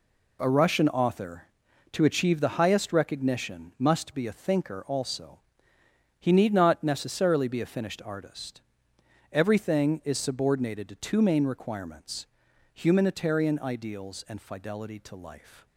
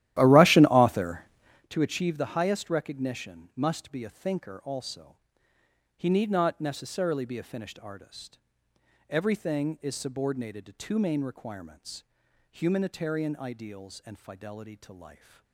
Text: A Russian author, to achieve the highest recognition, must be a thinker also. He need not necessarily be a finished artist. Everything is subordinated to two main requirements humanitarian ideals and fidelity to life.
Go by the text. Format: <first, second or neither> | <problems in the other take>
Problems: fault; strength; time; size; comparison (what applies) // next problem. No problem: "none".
first | starts louder than the rest; strong; until 1.7 s; 13.5 dB // pauses between "requirements" and "humanitarian"; noticeable; at 12.0 s; 0.48 s long; noticeable in the first